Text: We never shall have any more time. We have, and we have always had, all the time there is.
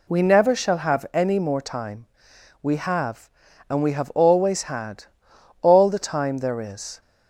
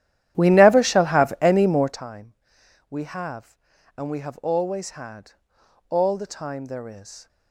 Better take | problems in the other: first | starts louder than the rest; strong; until 2.0 s; 12 dB

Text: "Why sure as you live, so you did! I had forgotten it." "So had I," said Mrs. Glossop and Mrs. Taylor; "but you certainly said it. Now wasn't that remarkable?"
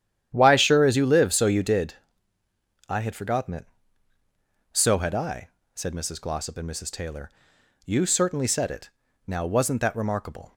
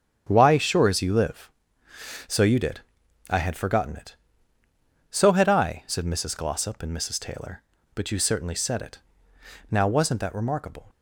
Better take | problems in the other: second | starts louder than the rest; strong; until 1.3 s; 10.5 dB; strong in the second // skips "but"; at 7.5 s

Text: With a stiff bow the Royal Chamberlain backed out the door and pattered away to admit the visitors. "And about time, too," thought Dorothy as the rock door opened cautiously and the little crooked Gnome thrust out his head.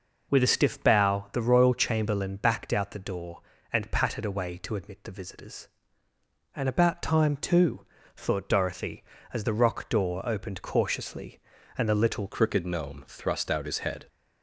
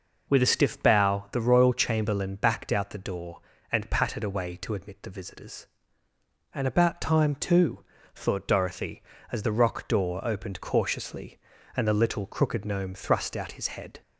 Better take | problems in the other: second | changes voice at "crooked"; from 12.3 s on; 1.7 s long

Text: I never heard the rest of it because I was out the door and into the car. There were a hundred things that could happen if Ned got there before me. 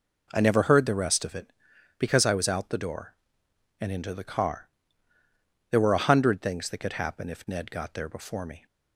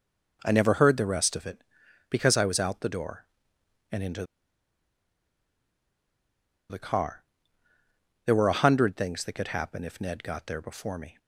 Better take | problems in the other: first | pauses between "into" and "the"; strong; at 4.2 s; 2.4 s long

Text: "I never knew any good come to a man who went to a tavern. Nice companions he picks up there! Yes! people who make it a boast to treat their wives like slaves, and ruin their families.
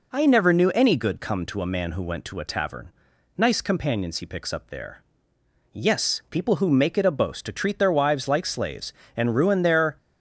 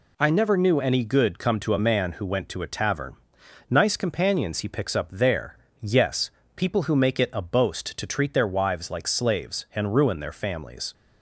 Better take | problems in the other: second | stops before "families"; at 9.9 s

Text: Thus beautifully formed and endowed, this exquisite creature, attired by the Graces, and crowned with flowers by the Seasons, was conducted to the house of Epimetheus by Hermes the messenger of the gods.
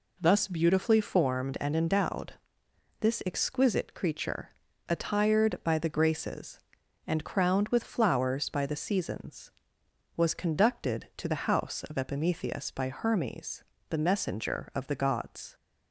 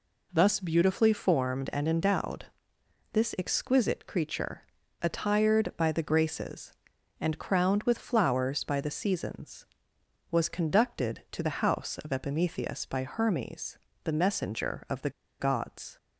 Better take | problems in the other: first | pauses between "Hermes" and "the"; slight; at 13.7 s; 0.26 s long; slight in the first // pauses between "the" and "gods"; slight; at 15.0 s; 0.30 s long

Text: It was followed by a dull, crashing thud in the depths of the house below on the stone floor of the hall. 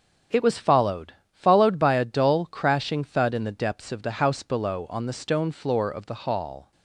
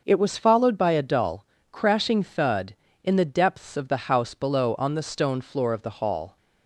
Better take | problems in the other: second | starts louder than the rest; strong; until 1.5 s; 7.5 dB; noticeable in the second // says "followed" twice; at 1.3 s

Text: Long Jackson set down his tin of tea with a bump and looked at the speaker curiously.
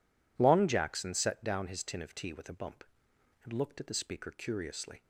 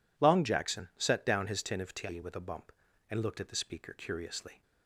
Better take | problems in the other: neither | none

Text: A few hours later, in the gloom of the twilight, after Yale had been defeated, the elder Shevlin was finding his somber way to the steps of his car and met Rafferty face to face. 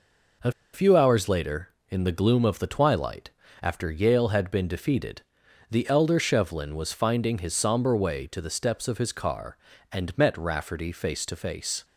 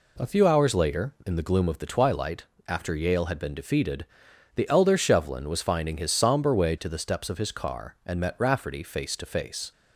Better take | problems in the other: second | pauses between "A" and "few"; slight; at 0.5 s; 0.21 s long

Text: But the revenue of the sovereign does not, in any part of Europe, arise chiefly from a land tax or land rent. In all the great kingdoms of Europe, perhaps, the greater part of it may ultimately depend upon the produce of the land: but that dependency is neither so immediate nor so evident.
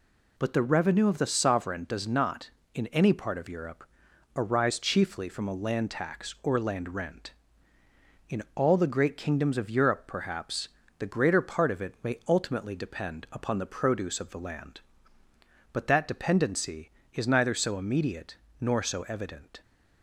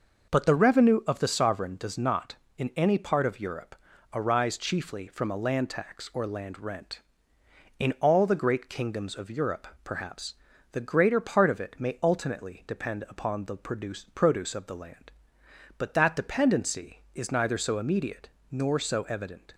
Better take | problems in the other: first | says "produce" twice; at 14.1 s // pauses between "immediate" and "nor"; slight; at 18.2 s; 0.22 s long; slight in the first

